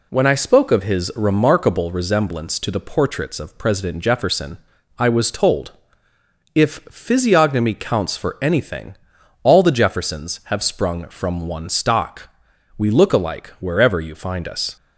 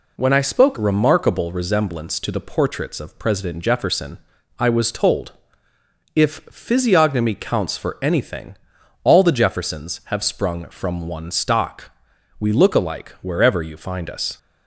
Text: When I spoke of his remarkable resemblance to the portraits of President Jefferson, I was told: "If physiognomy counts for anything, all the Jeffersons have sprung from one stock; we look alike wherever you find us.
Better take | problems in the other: first | skips "of his"; at 0.7 s

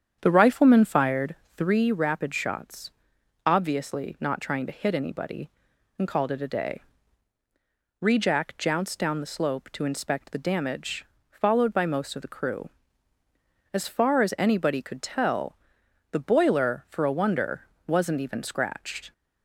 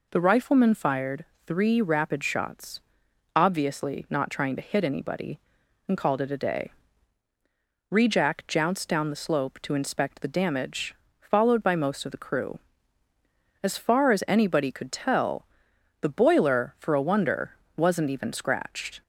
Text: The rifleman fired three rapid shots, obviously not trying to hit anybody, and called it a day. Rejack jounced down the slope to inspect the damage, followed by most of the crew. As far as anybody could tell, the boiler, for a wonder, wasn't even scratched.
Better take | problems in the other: second | starts louder than the rest; strong; until 1.9 s; 8.5 dB // pauses between "fired" and "three"; slight; at 1.3 s; 0.20 s long; slight in the second

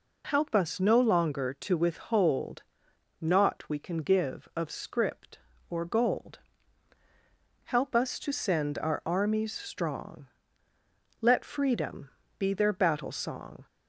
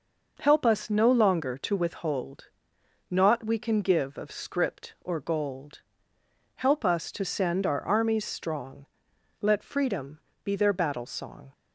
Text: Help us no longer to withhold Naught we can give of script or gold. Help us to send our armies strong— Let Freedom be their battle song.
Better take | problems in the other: neither | pauses between "withhold" and "Naught"; noticeable; the same in both // pauses between "Freedom" and "be"; slight; the same in both

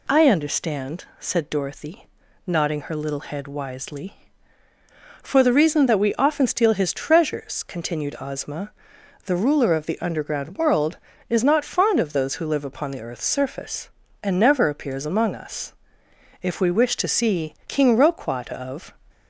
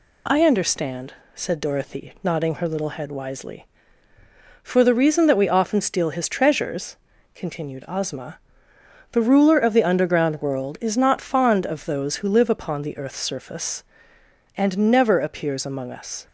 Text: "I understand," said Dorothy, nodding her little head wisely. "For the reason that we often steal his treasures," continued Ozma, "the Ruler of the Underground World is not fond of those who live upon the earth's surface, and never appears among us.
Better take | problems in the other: second | goes on to say "If we wish to see King Roquat of"; strong; from 16.4 s on; 2.5 s long

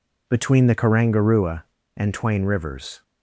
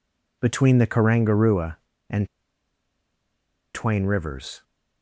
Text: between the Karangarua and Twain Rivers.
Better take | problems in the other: first | pauses between "and" and "Twain"; strong; at 2.2 s; 1.4 s long

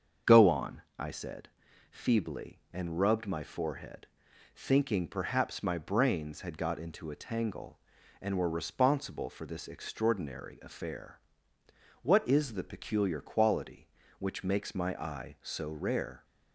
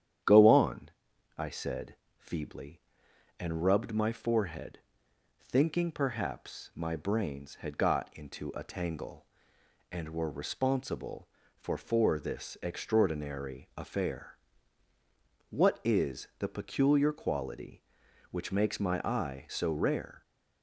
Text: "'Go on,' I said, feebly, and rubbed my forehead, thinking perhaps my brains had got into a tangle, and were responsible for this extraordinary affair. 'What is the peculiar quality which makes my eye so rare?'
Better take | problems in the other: first | starts louder than the rest; strong; until 1.6 s; 9.5 dB; strong in the first // says "for" twice; at 11.7 s

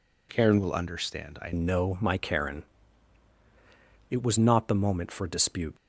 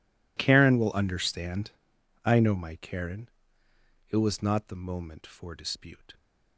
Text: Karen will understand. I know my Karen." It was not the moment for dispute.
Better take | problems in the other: second | changes voice at "know"; from 1.5 s on; 4.2 s long

